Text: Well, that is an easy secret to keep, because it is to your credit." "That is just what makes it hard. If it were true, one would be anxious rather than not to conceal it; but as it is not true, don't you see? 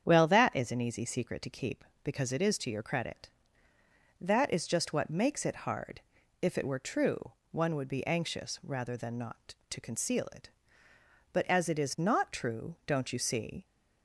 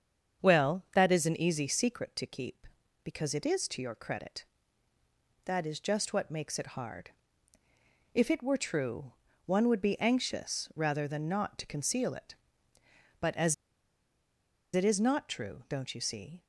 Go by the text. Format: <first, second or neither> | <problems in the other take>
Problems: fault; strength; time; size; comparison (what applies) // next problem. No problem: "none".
first | starts louder than the rest; strong; until 1.5 s; 7.5 dB; strong in the first // pauses between "as" and "it"; at 13.5 s; 1.1 s long